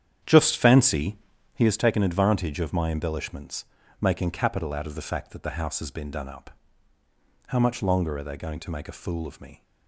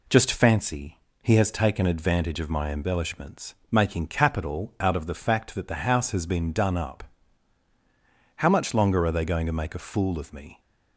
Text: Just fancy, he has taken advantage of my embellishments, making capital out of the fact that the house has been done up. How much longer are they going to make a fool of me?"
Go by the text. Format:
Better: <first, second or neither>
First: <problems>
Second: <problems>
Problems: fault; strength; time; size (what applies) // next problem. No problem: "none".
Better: second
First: starts louder than the rest; strong; until 1.6 s; 9 dB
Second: none